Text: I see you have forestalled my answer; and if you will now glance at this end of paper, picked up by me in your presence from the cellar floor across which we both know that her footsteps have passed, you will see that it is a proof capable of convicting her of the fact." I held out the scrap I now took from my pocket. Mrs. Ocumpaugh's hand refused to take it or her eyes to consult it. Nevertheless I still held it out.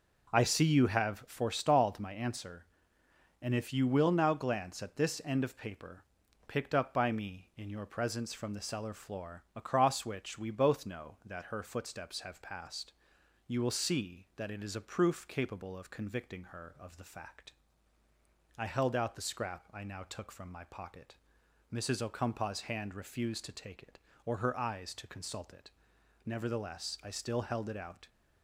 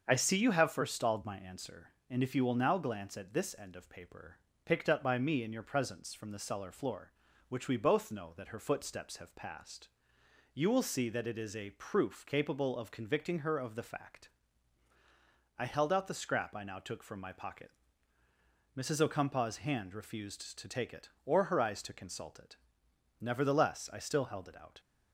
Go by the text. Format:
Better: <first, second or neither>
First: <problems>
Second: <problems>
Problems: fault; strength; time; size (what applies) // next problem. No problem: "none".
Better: first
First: none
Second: starts louder than the rest; until 1.0 s; 6.5 dB // skips "across"; at 7.3 s